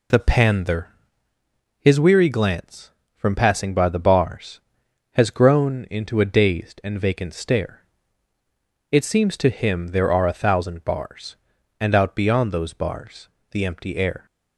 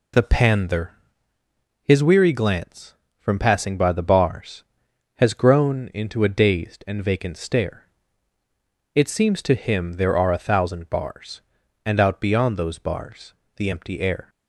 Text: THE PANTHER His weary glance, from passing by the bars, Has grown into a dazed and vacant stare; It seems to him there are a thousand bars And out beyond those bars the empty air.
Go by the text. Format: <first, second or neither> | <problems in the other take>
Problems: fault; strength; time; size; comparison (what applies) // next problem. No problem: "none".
neither | pauses between "PANTHER" and "His"; noticeable; the same in both // pauses between "bars" and "the"; slight; the same in both